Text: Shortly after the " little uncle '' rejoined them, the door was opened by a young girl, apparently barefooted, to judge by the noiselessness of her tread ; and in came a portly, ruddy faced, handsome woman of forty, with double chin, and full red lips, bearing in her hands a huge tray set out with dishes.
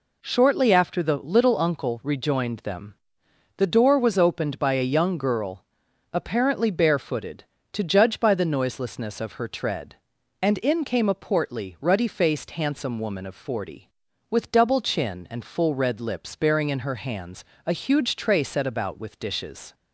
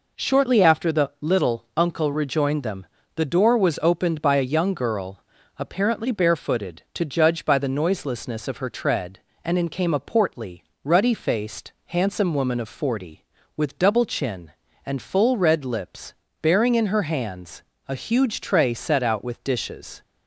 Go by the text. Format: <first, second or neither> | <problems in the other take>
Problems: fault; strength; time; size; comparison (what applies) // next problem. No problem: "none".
second | pauses between "hands" and "a"; slight; at 17.4 s; 0.22 s long; slight in the second // says "about" for "out"; at 18.6 s